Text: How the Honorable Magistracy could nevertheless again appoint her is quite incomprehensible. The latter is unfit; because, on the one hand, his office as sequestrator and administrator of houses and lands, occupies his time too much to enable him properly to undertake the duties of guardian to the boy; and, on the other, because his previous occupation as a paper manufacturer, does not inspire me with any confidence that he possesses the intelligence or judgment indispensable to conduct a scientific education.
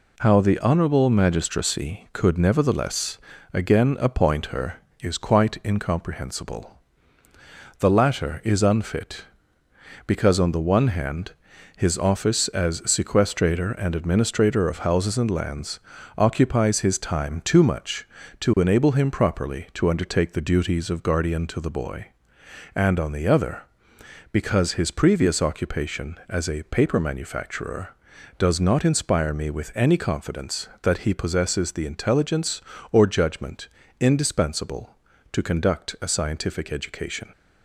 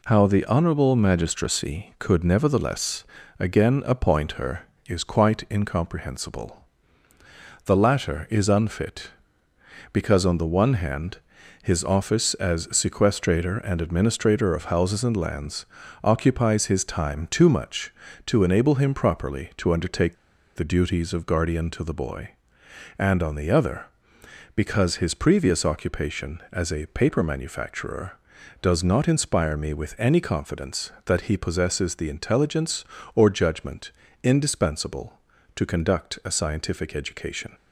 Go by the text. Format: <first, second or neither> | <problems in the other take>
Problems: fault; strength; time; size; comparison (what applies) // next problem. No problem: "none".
first | pauses between "nevertheless" and "again"; slight; at 3.0 s; 0.34 s long; slight in the first // pauses between "undertake" and "the"; at 20.1 s; 0.41 s long // pauses between "judgment" and "indispensable"; slight; at 33.9 s; 0.28 s long; slight in the first